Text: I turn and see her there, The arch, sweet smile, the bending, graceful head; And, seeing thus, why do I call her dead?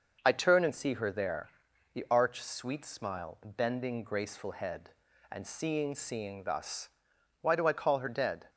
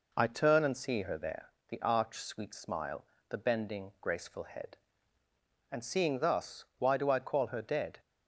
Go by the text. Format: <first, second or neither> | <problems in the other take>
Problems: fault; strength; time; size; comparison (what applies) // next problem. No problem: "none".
second | says "seeing" twice; at 5.9 s